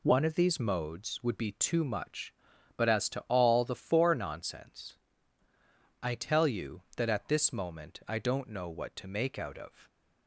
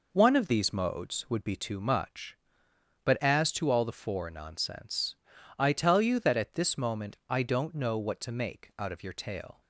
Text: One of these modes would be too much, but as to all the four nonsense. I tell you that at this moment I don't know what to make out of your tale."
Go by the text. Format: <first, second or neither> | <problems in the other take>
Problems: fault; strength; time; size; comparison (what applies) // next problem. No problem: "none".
second | stops before "your tale"; at 9.8 s